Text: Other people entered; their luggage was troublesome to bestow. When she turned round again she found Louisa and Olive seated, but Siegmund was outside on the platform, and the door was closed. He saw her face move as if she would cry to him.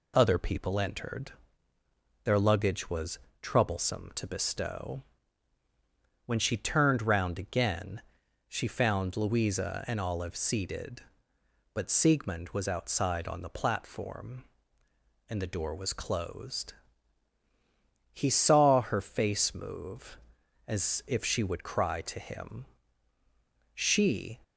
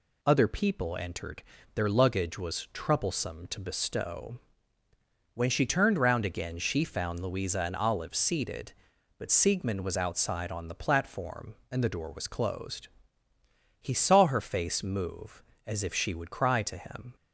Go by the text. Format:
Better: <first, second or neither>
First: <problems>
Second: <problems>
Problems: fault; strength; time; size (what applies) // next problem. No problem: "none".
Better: second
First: pauses between "was" and "troublesome"; slight; at 3.1 s; 0.22 s long // pauses between "again" and "she"; noticeable; at 8.0 s; 0.46 s long // goes on to say "She"; noticeable; from 23.7 s on; 0.64 s long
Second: none